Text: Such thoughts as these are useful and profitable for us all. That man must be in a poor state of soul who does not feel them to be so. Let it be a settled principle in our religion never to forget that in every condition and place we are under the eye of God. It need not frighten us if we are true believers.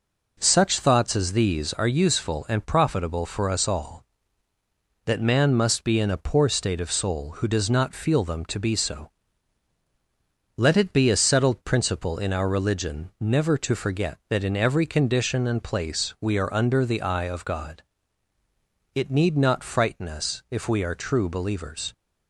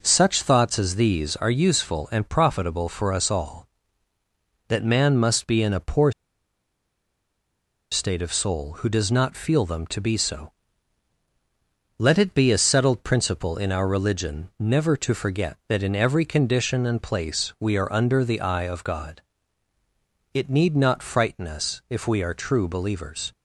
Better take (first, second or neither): first